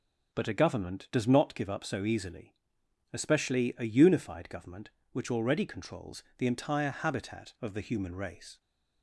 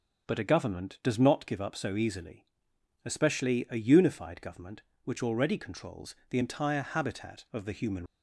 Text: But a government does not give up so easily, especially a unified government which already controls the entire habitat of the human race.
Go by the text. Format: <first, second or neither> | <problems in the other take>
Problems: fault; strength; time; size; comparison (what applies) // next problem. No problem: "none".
first | stops before "race"; at 8.0 s